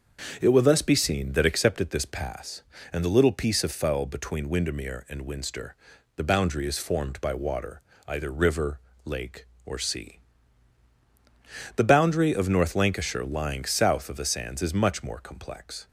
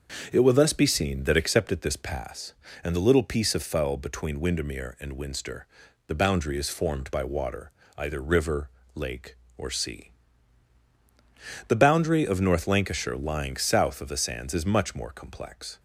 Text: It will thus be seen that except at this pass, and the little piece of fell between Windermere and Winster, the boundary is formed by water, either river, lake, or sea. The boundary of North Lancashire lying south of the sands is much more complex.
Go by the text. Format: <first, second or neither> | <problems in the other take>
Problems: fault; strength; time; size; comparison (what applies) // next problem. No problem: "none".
neither | starts louder than the rest; the same in both